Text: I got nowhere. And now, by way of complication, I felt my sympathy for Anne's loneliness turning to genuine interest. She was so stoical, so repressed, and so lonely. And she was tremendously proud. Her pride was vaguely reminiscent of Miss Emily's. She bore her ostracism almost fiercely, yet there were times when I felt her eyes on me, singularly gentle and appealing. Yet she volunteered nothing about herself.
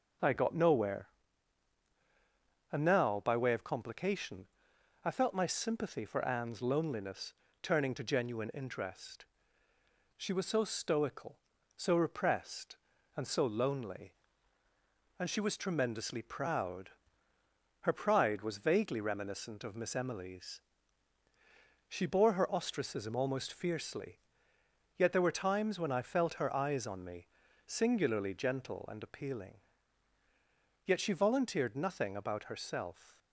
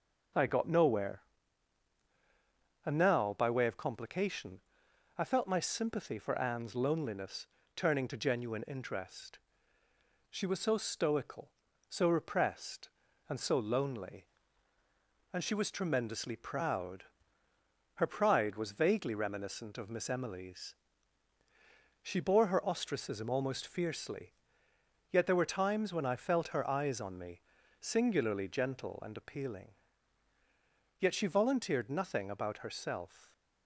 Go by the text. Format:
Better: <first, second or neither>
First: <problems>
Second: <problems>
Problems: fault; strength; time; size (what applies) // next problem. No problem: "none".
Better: neither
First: pauses between "loneliness" and "turning"; slight; at 7.3 s; 0.28 s long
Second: pauses between "loneliness" and "turning"; slight; at 7.4 s; 0.28 s long